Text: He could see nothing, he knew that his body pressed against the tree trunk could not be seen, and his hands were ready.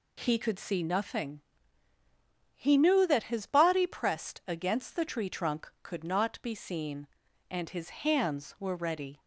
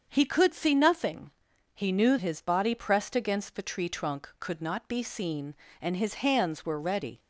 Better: first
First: none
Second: starts louder than the rest; until 1.1 s; 7 dB // skips "that"; at 2.1 s

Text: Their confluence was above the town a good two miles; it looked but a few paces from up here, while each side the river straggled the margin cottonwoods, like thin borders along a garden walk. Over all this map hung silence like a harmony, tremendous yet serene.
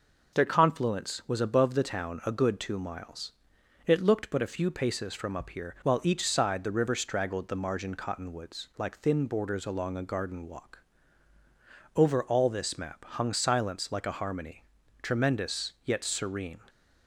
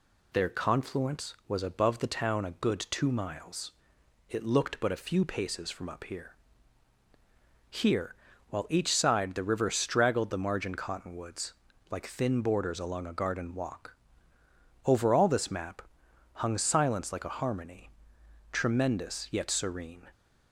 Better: first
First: none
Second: says "here" twice; at 7.6 s // pauses between "map" and "hung"; noticeable; at 15.8 s; 0.54 s long

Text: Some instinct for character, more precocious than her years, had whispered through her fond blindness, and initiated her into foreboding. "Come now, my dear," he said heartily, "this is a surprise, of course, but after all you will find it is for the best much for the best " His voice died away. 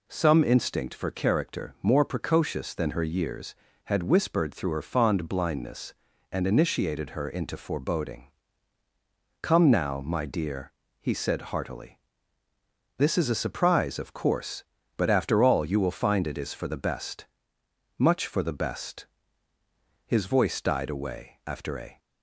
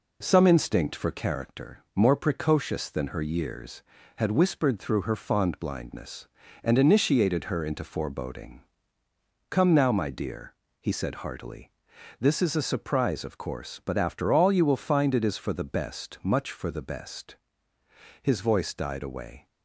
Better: second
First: pauses between "best" and "much"; noticeable; at 17.2 s; 0.72 s long // goes on to say "After a"; from 21.4 s on; 0.52 s long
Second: none

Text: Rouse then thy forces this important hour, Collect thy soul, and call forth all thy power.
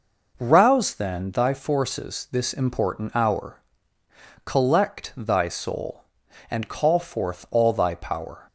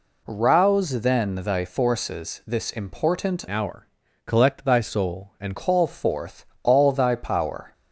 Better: first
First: none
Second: changes voice from "hour" to "and"; from 3.4 to 5.5 s; 2.1 s long // pauses between "forth" and "all"; slight; at 6.4 s; 0.20 s long

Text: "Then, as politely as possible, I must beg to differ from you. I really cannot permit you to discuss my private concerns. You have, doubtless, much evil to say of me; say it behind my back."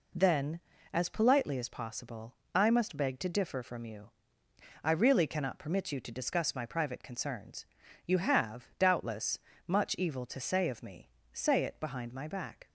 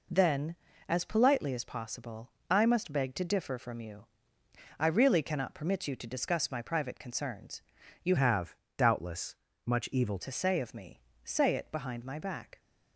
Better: first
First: none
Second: changes voice from "have" to "evil"; from 8.1 to 10.1 s; 2.0 s long

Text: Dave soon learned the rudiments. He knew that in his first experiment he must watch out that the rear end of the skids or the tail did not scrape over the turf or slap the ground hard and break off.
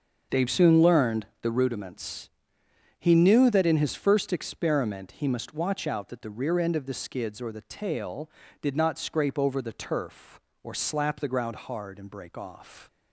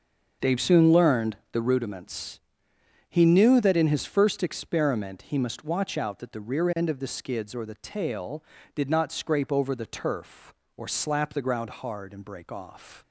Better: neither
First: starts louder than the rest; until 1.4 s; 6.5 dB // pauses between "learned" and "the"; slight; at 1.2 s; 0.16 s long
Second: starts louder than the rest; until 1.5 s; 6.5 dB // pauses between "learned" and "the"; slight; at 1.3 s; 0.16 s long

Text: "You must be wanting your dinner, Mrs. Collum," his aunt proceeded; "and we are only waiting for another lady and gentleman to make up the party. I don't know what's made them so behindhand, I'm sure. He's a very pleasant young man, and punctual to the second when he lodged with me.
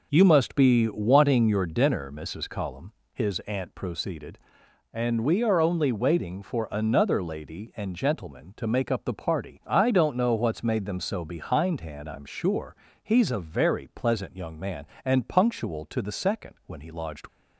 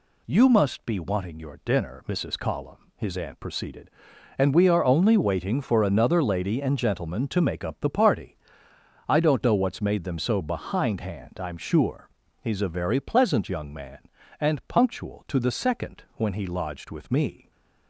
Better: second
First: stops before "with me"; at 17.2 s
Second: none

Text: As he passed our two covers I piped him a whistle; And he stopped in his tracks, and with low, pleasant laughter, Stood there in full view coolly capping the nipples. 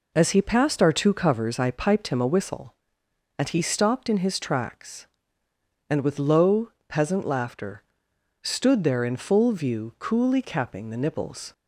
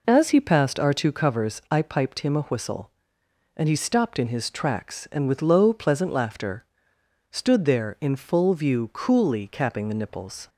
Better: second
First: says "peasant" for "pleasant"; at 6.8 s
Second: none

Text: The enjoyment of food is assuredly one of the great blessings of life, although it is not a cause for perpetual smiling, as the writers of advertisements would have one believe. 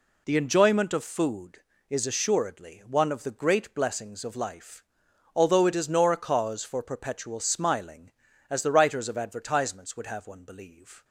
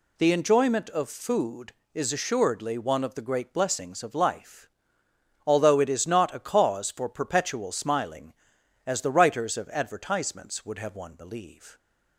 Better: second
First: says "nor" for "not"; at 5.8 s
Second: none

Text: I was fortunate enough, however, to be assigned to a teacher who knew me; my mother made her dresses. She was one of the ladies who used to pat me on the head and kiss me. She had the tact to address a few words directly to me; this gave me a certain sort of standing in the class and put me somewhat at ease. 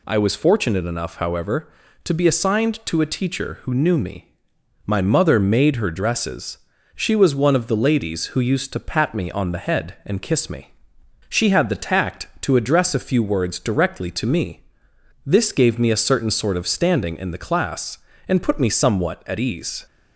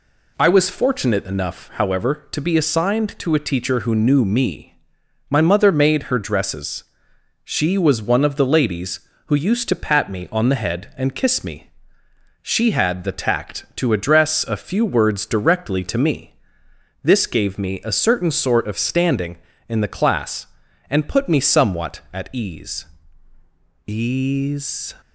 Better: first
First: none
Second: says "ease" twice; at 23.8 s

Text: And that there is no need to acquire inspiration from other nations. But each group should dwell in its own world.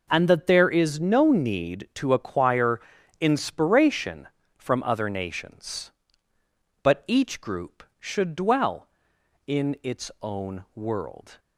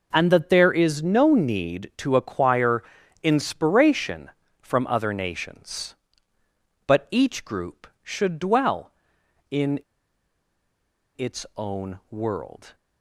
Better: first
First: pauses between "acquire" and "inspiration"; at 2.8 s; 0.40 s long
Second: pauses between "acquire" and "inspiration"; at 2.8 s; 0.40 s long // pauses between "in" and "its"; strong; at 9.7 s; 1.3 s long

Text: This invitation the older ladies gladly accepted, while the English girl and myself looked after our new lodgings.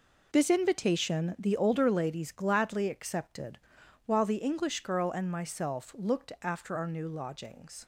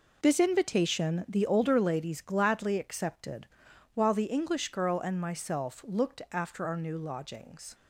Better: neither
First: none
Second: none

